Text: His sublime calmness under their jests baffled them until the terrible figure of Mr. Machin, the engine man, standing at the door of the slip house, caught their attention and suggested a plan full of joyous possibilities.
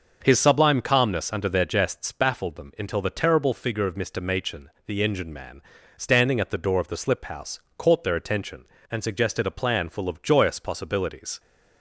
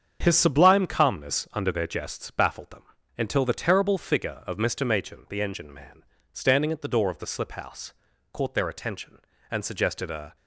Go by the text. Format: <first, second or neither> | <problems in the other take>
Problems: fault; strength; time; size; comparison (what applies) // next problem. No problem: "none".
first | starts louder than the rest; strong; until 1.2 s; 7.5 dB; noticeable in the first // pauses between "them" and "until"; slight; at 2.8 s; 0.34 s long // stops before "plan full of joyous possibilities"; at 10.3 s